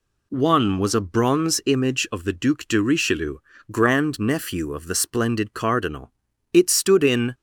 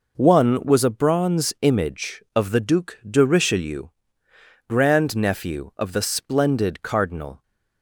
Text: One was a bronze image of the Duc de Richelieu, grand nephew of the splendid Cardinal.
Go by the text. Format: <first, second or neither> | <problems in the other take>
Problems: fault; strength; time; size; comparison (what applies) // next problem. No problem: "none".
second | goes on to say "It stood in"; noticeable; from 6.5 s on; 0.80 s long